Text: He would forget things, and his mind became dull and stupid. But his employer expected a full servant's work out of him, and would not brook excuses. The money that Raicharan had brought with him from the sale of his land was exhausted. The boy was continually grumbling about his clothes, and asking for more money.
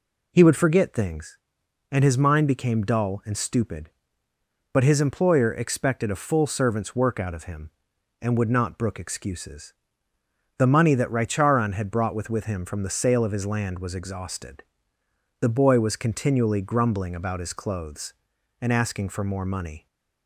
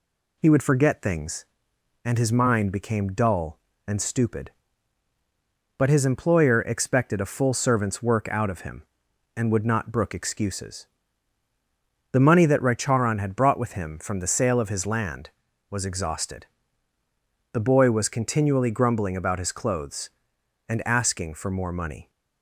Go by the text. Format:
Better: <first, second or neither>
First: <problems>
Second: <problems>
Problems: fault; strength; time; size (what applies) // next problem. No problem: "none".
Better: second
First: says "with" twice; at 12.3 s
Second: none